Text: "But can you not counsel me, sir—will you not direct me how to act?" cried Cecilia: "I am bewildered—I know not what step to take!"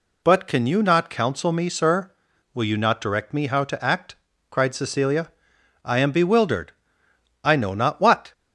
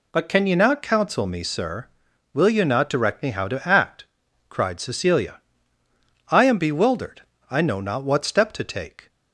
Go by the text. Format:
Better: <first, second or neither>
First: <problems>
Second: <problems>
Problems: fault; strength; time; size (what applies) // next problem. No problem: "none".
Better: second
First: stops before "step to take"; at 8.3 s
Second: none